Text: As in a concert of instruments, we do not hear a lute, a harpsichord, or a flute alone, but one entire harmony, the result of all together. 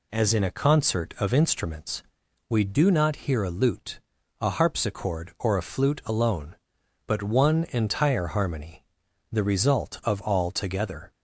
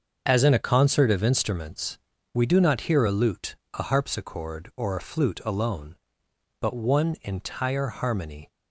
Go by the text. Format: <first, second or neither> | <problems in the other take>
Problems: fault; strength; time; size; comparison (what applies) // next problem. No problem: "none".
first | starts louder than the rest; until 1.2 s; 6.5 dB // stops before "the result of all together"; at 8.4 s